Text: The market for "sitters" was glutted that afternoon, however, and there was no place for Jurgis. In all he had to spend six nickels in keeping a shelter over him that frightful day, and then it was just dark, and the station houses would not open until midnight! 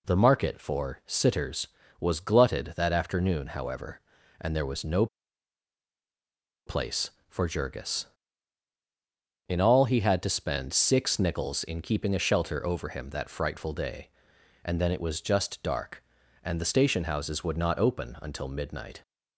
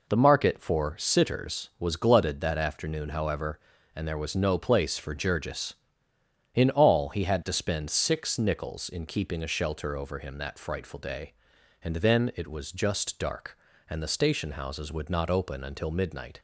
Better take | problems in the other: second | pauses between "no" and "place"; strong; at 5.0 s; 1.6 s long

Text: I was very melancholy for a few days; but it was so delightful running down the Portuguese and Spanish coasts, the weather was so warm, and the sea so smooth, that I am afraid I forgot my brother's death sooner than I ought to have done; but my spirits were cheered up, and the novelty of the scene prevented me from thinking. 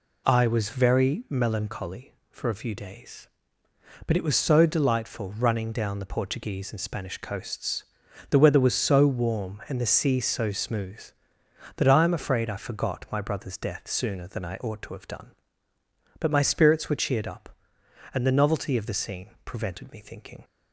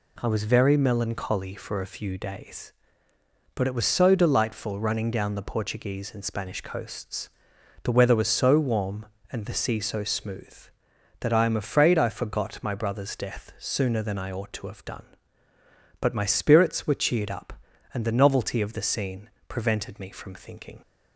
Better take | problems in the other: second | pauses between "scene" and "prevented"; slight; at 19.2 s; 0.16 s long; slight in the second // skips "from"; at 19.9 s

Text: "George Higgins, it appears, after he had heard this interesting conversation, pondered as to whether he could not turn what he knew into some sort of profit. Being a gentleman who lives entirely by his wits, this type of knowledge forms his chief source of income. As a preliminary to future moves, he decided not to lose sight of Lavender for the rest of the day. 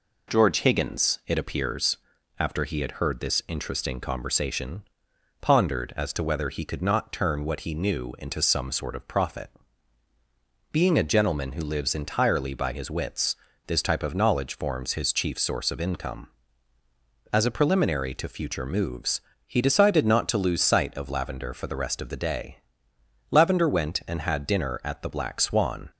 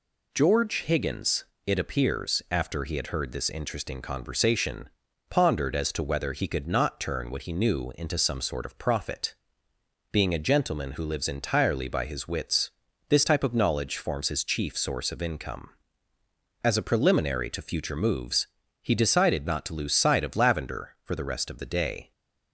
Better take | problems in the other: second | goes on to say "Lavender went and had dinner at The Black Swan"; strong; from 23.3 s on; 2.5 s long

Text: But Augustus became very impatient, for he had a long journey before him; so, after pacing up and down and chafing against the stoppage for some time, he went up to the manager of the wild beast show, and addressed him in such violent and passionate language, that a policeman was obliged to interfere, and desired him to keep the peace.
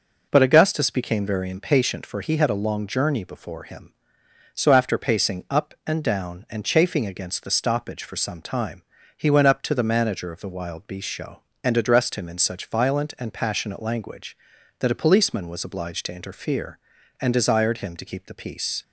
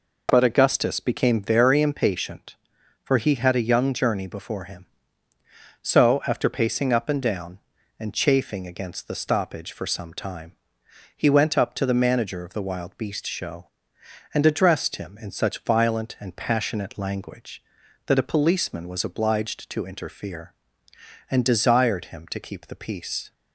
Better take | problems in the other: first | says "young" for "long"; at 3.6 s

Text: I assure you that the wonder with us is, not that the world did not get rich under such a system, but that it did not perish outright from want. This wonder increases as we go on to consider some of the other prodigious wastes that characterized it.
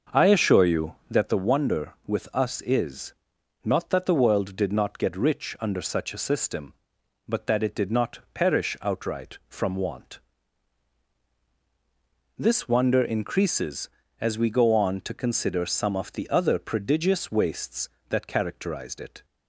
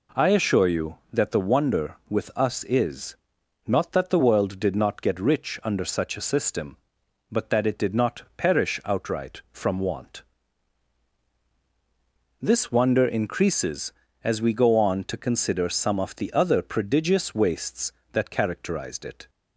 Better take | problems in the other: second | starts louder than the rest; until 1.3 s; 6.5 dB

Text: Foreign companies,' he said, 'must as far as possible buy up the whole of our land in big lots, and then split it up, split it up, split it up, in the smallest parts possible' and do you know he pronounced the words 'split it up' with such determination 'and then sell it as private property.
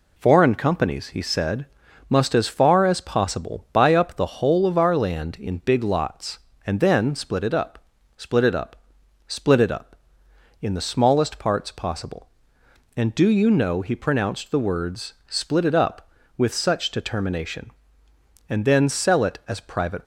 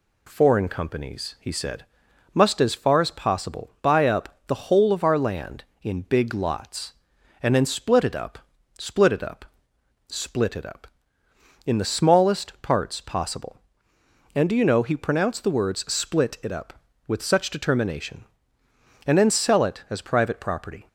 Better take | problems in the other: second | stops before "property"; at 20.0 s

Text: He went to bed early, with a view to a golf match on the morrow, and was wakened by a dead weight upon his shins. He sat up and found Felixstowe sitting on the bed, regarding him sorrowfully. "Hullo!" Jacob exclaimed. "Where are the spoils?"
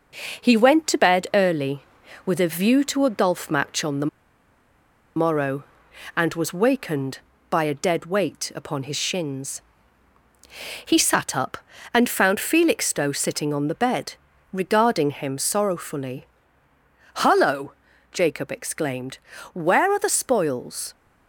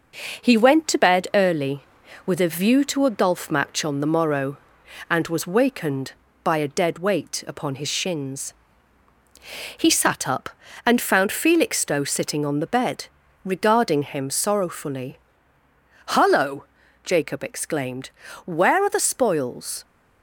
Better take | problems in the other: second | pauses between "the" and "morrow"; at 4.0 s; 1.0 s long

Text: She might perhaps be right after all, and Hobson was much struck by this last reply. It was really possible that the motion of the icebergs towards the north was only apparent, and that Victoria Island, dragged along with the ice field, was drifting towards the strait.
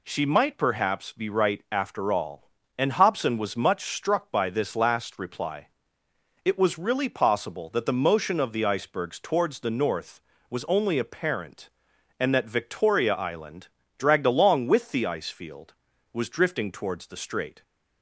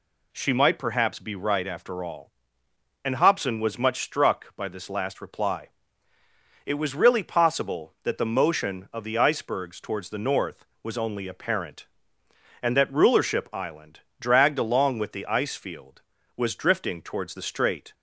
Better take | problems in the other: first | says "Rulership" for "Victoria"; at 12.9 s

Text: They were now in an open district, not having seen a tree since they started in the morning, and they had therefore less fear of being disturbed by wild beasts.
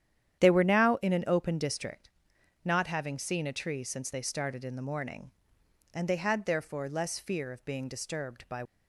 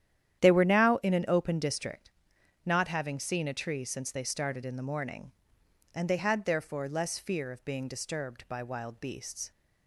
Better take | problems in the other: second | starts louder than the rest; strong; until 1.4 s; 10 dB; strong in the second // stops before "wild beasts"; at 8.6 s

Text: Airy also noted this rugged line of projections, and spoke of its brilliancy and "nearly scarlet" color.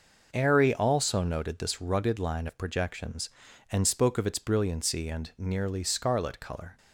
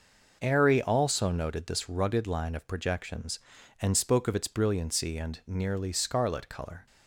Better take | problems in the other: neither | none

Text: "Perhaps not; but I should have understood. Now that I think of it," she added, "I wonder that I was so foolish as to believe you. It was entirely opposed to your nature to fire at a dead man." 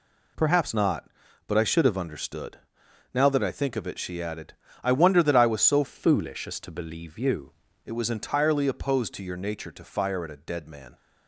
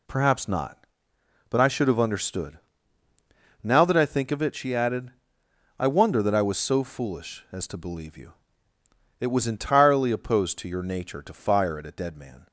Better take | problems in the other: second | changes voice from "foolish" to "you"; from 5.8 to 7.5 s; 1.7 s long

